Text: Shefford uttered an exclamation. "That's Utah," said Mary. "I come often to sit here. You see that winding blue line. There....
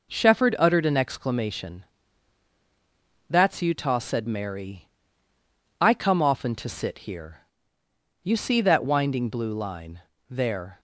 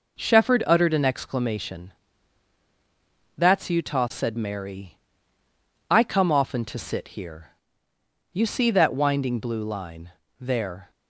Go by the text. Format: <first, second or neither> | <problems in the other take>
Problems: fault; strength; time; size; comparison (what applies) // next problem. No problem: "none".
neither | none